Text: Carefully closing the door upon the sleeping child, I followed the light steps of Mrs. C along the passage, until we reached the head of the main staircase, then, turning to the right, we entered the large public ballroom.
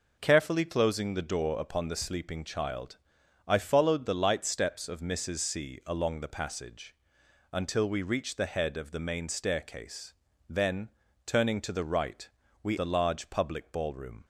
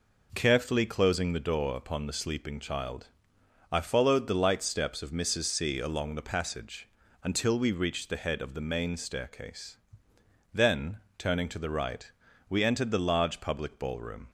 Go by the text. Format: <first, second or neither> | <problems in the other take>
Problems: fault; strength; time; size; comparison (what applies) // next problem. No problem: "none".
second | skips "entered"; at 12.7 s